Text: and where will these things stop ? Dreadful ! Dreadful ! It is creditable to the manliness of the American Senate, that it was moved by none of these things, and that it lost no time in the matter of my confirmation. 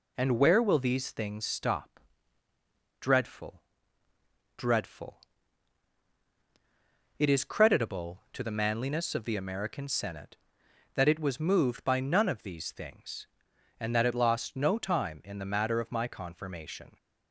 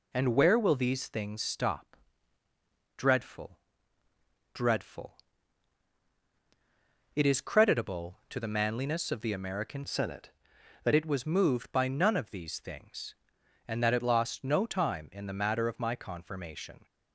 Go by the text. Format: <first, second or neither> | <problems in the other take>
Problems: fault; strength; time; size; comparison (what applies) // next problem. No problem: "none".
first | changes voice from "Senate" to "that"; from 9.8 to 10.9 s; 1.1 s long